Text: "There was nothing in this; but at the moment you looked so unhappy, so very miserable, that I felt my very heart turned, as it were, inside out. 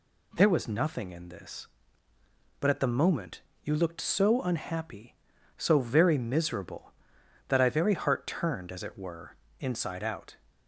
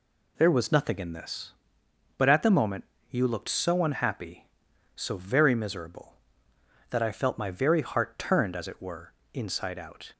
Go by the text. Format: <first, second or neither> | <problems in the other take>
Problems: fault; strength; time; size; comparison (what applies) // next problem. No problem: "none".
second | pauses between "moment" and "you"; slight; at 3.4 s; 0.22 s long; slight in the second // skips "felt my"; at 7.6 s